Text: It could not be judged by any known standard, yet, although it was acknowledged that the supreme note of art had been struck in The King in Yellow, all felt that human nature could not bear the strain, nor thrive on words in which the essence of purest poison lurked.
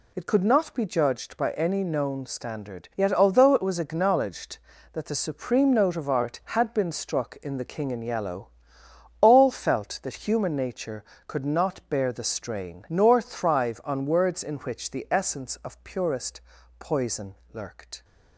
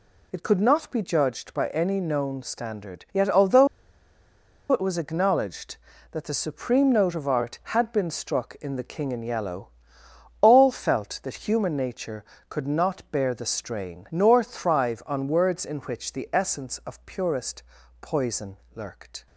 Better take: first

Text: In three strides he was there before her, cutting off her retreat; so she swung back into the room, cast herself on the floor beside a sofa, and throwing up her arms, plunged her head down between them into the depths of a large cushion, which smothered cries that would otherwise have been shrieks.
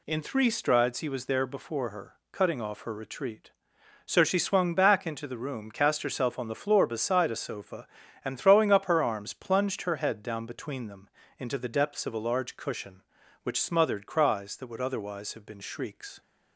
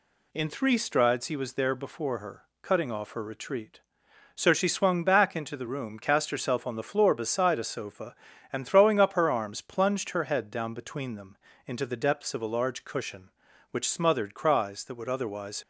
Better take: first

